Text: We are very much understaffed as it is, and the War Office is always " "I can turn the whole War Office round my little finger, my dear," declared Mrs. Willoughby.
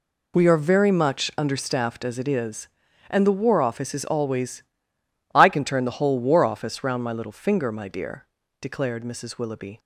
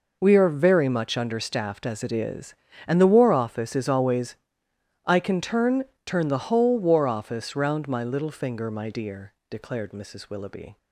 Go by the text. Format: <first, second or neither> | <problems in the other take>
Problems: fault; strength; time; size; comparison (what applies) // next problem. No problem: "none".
first | says "turn" twice; at 6.0 s